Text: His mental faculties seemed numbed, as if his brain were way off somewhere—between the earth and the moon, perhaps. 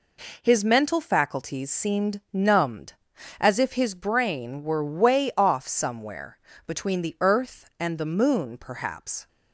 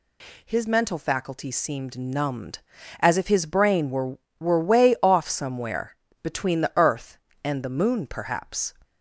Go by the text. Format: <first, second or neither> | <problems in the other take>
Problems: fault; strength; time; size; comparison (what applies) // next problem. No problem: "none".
first | says "were" twice; at 4.3 s